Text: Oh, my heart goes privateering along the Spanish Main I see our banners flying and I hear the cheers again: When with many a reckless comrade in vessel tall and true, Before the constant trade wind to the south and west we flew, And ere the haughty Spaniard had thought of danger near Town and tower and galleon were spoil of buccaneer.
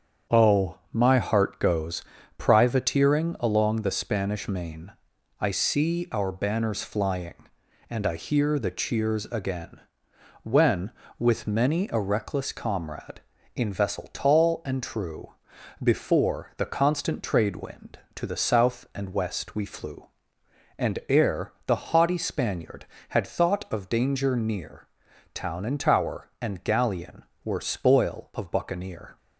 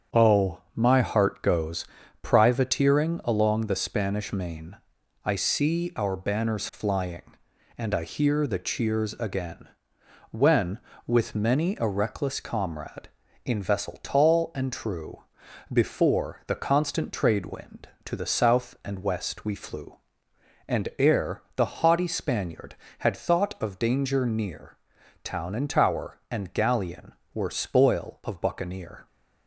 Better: neither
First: starts louder than the rest; strong; until 1.4 s; 8 dB // pauses between "goes" and "privateering"; slight; at 2.0 s; 0.33 s long // pauses between "Main" and "I"; noticeable; at 4.8 s; 0.50 s long // pauses between "near" and "Town"; noticeable; at 24.8 s; 0.48 s long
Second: starts louder than the rest; strong; until 1.2 s; 8 dB // pauses between "goes" and "privateering"; slight; at 1.8 s; 0.34 s long // pauses between "Main" and "I"; noticeable; at 4.7 s; 0.50 s long // pauses between "near" and "Town"; noticeable; at 24.7 s; 0.48 s long

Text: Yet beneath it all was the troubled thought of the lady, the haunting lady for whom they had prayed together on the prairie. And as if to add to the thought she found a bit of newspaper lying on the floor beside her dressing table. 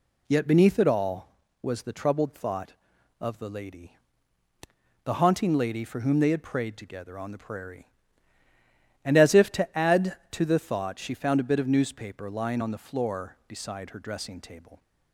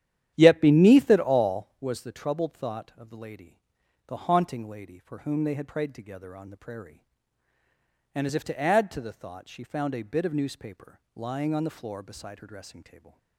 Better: first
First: none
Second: starts louder than the rest; strong; until 1.9 s; 10.5 dB // pauses between "newspaper" and "lying"; slight; at 10.9 s; 0.16 s long // stays silent after the last word; slight; from 12.8 s on; 0.5 s long

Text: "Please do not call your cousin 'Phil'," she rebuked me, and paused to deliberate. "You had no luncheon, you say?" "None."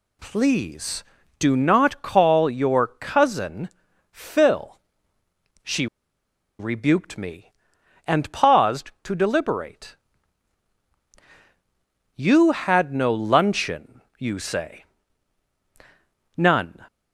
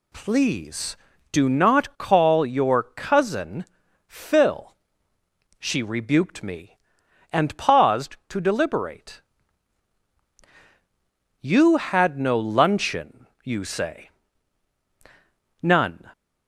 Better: second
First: pauses between "cousin" and "Phil"; at 3.7 s; 0.42 s long // pauses between "she" and "rebuked"; noticeable; at 5.8 s; 0.73 s long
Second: pauses between "cousin" and "Phil"; at 3.6 s; 0.42 s long

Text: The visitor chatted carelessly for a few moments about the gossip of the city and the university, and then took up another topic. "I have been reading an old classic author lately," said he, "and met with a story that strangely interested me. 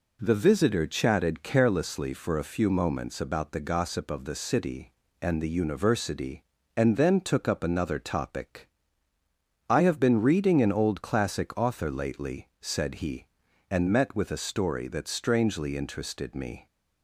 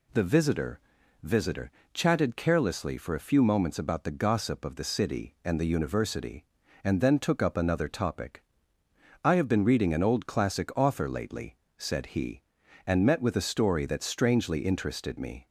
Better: first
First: none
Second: says "visitor" twice; at 1.2 s

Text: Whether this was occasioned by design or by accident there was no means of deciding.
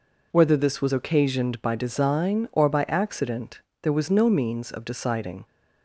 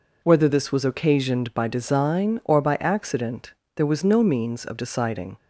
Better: neither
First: pauses between "accident" and "there"; slight; at 3.6 s; 0.22 s long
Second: pauses between "accident" and "there"; slight; at 3.5 s; 0.24 s long

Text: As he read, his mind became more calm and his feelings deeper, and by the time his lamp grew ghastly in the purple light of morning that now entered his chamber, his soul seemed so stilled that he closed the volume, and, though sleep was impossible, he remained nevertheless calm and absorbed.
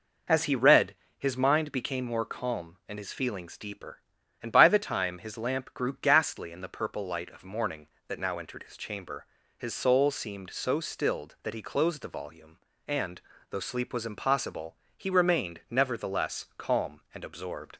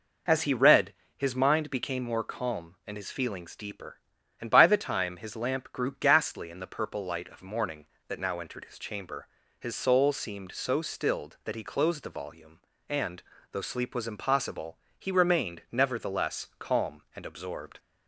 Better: neither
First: none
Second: none

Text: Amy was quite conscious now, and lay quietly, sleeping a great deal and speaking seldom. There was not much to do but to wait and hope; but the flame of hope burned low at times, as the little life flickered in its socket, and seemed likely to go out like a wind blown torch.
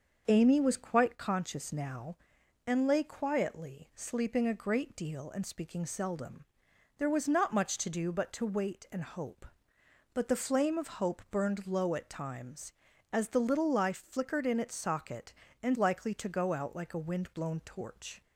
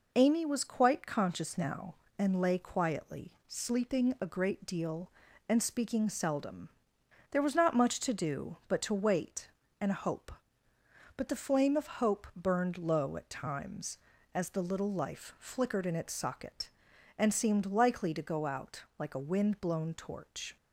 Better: second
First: starts louder than the rest; until 1.2 s; 6.5 dB // skips "seemed"; at 15.7 s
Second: none

